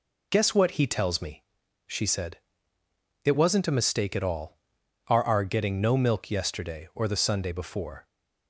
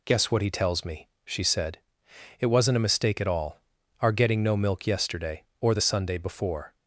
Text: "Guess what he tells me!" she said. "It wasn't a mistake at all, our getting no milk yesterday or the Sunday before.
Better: second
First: says "our" twice; at 5.2 s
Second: none

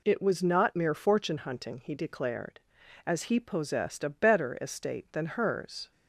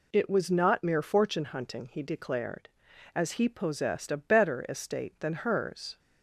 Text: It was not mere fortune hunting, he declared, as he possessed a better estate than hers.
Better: neither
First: none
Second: none

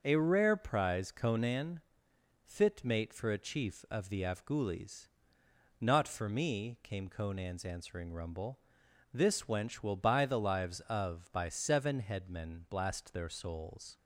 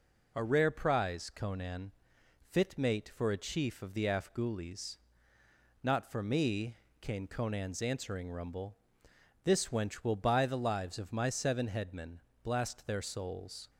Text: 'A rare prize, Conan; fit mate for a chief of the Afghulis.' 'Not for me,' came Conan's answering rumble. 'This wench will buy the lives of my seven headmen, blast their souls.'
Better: second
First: starts louder than the rest; until 1.0 s; 6.5 dB // says "by" for "my"; at 11.3 s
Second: none

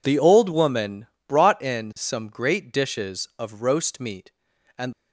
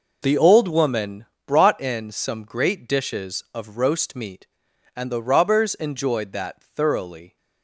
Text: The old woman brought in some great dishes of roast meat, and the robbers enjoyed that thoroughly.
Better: second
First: pauses between "woman" and "brought"; slight; at 1.0 s; 0.20 s long // stops before "the robbers enjoyed that thoroughly"; at 4.9 s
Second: pauses between "woman" and "brought"; slight; at 1.2 s; 0.20 s long

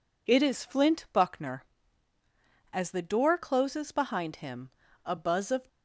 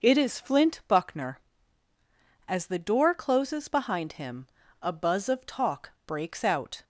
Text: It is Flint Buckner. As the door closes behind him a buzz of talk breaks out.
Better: second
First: pauses between "him" and "a"; slight; at 4.7 s; 0.34 s long // stops before "talk breaks out"; at 5.6 s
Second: pauses between "him" and "a"; slight; at 4.4 s; 0.34 s long

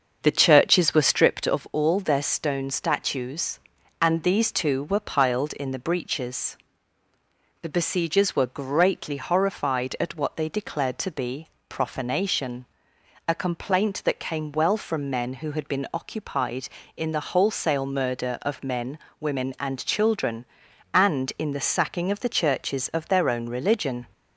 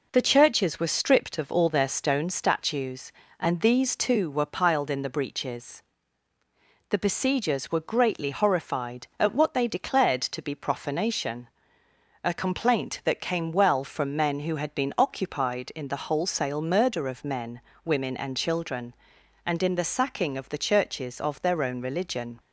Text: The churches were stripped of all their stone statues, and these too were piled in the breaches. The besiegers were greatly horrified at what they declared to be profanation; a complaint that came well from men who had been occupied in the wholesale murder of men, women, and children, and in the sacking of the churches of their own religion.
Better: second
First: starts louder than the rest; until 1.5 s; 6.5 dB // pauses between "be" and "profanation"; slight; at 11.4 s; 0.22 s long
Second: none

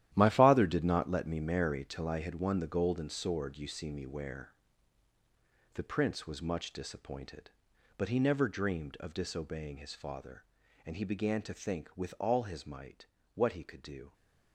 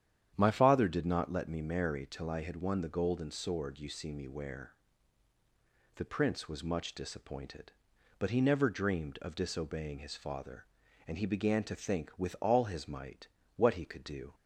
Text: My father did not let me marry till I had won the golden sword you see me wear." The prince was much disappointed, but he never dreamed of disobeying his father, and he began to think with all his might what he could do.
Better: second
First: gets quieter; strong; throughout; 12 dB // starts louder than the rest; strong; until 1.1 s; 12.5 dB // pauses between "might" and "what"; slight; at 13.0 s; 0.26 s long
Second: starts louder than the rest; strong; until 1.3 s; 9.5 dB // pauses between "might" and "what"; slight; at 13.2 s; 0.26 s long

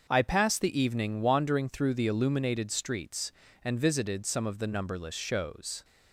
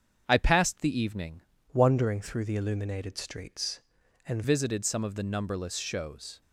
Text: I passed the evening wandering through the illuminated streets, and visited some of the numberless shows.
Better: first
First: starts louder than the rest; until 1.1 s; 6.5 dB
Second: starts louder than the rest; strong; until 1.2 s; 7.5 dB // changes voice from "wandering" to "and"; from 1.7 to 4.4 s; 2.7 s long

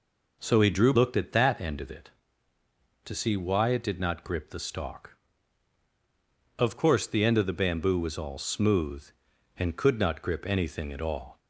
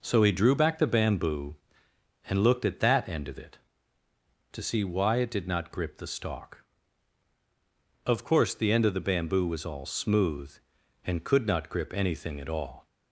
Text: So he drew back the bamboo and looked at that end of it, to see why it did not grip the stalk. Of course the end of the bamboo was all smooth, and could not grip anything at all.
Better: second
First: skips "back the bamboo and"; at 0.9 s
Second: none

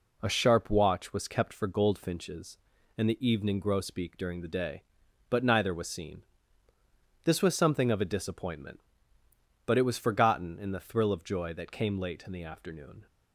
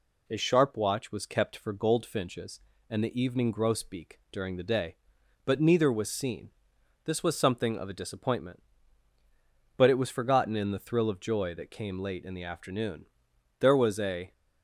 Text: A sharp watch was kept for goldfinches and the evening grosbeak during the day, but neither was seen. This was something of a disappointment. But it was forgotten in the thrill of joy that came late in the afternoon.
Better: first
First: none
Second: goes on to say "There was a"; noticeable; from 13.6 s on; 0.72 s long

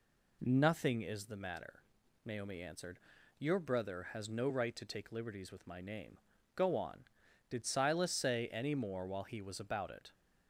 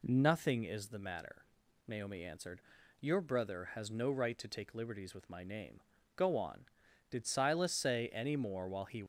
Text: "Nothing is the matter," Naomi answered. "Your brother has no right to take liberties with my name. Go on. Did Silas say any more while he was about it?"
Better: first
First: none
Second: stops before "was about it"; at 9.0 s

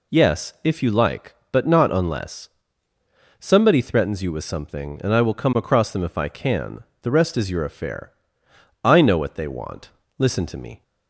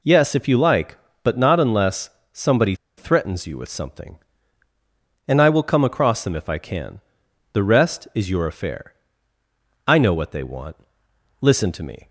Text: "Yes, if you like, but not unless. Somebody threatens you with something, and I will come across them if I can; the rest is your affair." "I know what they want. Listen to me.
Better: first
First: none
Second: pauses between "Somebody" and "threatens"; slight; at 2.7 s; 0.23 s long

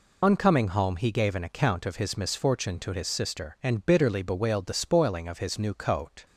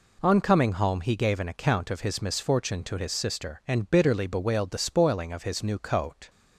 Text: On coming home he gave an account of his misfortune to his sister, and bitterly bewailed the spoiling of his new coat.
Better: second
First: loses the start of "On"; at 0.2 s; 85 ms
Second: none

